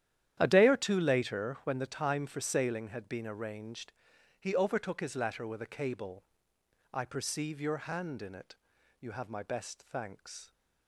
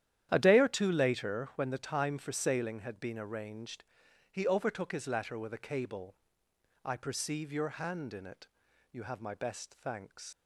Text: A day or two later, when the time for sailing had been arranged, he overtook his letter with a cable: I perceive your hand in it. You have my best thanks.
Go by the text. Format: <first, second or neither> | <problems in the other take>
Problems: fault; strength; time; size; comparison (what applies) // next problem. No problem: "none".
first | starts louder than the rest; strong; until 1.3 s; 11 dB; strong in the first // leaves "thanks" unfinished; at 10.3 s; 110 ms